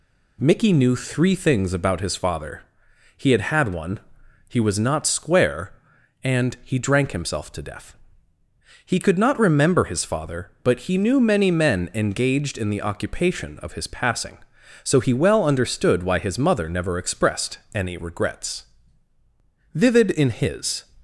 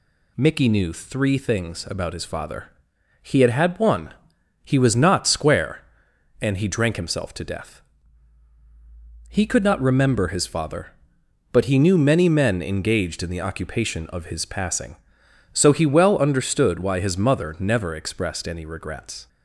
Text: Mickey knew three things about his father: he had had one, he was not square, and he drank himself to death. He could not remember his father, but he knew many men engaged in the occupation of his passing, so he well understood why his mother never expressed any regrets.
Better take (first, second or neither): second